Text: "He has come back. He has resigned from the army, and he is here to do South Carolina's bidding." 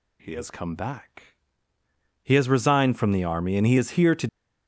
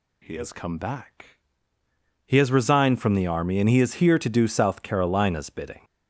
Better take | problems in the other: second | stops before "do South Carolina's bidding"; at 4.2 s

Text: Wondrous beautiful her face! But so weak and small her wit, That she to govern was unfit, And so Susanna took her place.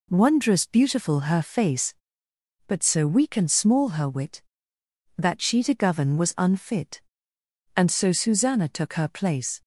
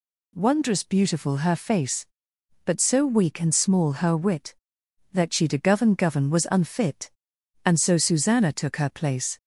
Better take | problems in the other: first | says "govern" twice; at 5.9 s

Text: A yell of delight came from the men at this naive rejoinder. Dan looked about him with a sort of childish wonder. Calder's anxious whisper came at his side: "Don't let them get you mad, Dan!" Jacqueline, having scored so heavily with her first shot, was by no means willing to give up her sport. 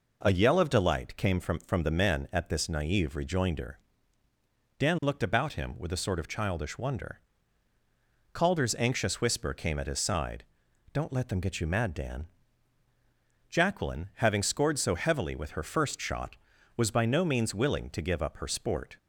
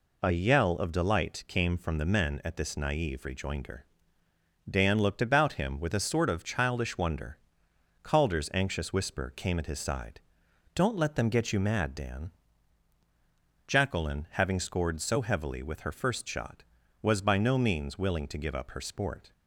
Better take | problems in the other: second | says "from" twice; at 1.5 s

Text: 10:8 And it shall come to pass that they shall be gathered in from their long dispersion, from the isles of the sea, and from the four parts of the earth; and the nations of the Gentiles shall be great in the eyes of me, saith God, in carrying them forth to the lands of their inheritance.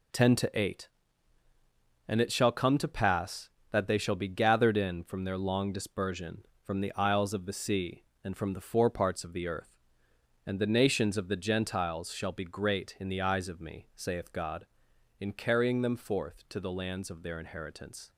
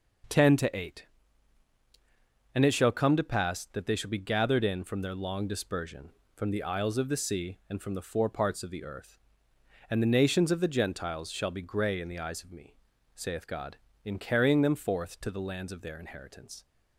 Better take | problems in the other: first | says "grey" for "great"; at 11.6 s

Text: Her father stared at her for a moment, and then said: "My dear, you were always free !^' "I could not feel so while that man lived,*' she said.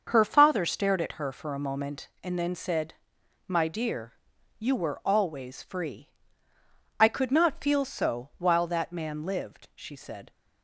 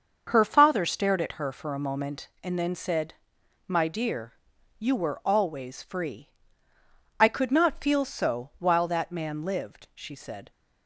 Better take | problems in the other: neither | starts louder than the rest; the same in both

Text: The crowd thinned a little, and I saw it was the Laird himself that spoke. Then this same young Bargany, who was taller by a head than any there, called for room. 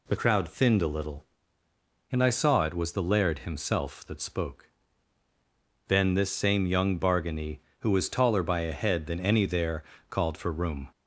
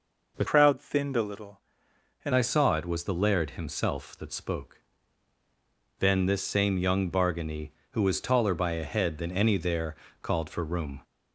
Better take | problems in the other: first | changes voice from "crowd" to "and"; from 0.4 to 2.3 s; 1.9 s long

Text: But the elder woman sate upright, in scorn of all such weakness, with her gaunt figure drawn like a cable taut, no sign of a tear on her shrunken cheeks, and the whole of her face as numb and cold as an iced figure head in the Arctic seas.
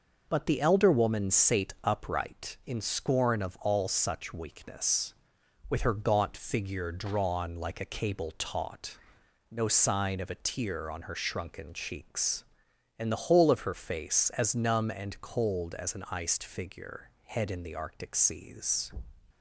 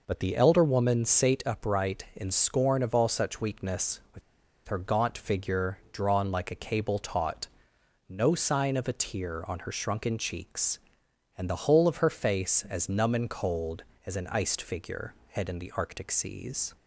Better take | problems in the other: first | pauses between "with" and "her"; noticeable; at 4.2 s; 0.46 s long // pauses between "figure" and "head"; slight; at 15.1 s; 0.18 s long; slight in the first

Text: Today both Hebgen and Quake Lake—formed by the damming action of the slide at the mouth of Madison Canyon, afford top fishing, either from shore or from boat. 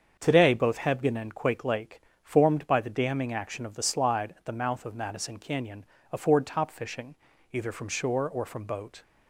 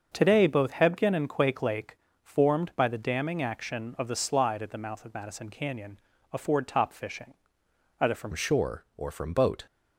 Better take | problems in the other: first | starts louder than the rest; until 1.1 s; 6.5 dB; strong in the first // changes voice at "shore"; from 8.3 s on; 1.3 s long

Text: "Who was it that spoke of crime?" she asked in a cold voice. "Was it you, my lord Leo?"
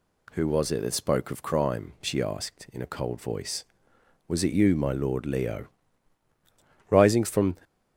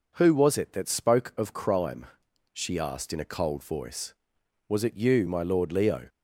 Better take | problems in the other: second | goes on to say "Rising from"; noticeable; from 6.8 s on; 0.66 s long

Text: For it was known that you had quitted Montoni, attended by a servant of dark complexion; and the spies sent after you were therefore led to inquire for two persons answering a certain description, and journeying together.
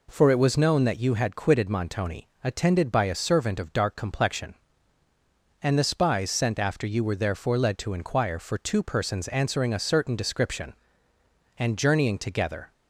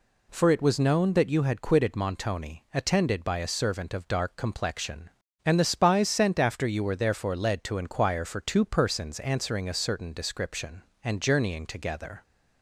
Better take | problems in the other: neither | none

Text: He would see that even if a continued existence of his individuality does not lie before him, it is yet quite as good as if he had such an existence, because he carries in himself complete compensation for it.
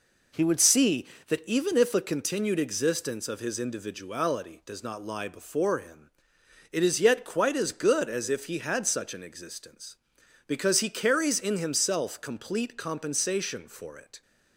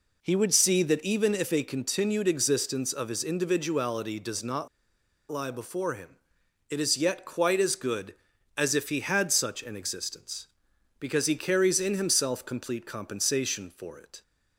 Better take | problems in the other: first | pauses between "not" and "lie"; noticeable; at 4.6 s; 0.63 s long

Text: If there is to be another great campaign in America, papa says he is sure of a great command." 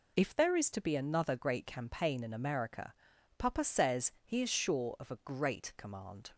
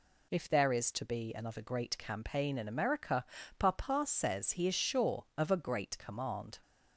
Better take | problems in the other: neither | none

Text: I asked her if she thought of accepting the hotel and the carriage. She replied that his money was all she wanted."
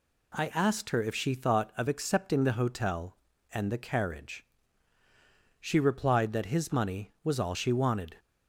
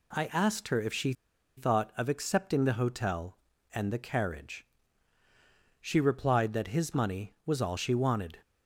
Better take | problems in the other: first | pauses between "she" and "thought"; at 1.1 s; 0.43 s long

